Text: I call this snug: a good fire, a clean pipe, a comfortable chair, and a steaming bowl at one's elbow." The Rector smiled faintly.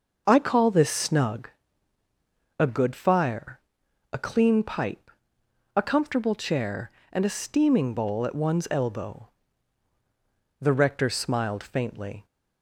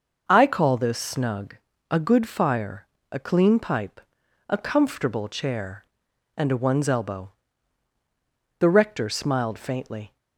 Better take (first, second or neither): first